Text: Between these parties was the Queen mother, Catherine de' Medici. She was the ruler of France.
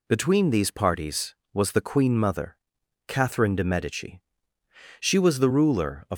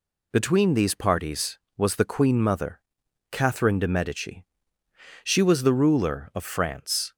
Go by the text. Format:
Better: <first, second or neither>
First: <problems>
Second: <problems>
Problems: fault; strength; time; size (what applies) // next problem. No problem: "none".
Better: second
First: stops before "France"; at 6.1 s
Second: none